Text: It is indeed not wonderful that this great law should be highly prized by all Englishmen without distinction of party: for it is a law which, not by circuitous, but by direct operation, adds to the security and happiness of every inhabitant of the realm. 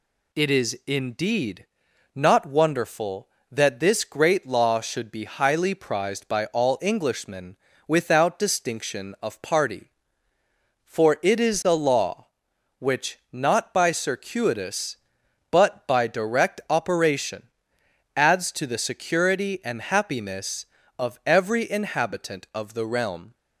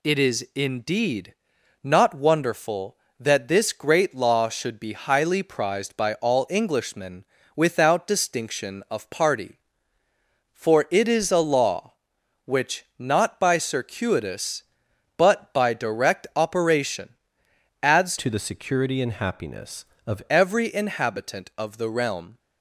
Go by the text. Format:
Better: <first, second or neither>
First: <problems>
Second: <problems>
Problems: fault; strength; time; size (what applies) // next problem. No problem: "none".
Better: first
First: pauses between "indeed" and "not"; noticeable; at 1.6 s; 0.48 s long // pauses between "Englishmen" and "without"; slight; at 7.5 s; 0.30 s long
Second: pauses between "indeed" and "not"; noticeable; at 1.3 s; 0.48 s long // pauses between "Englishmen" and "without"; slight; at 7.2 s; 0.30 s long // changes voice from "to" to "of"; from 18.1 to 20.2 s; 2.1 s long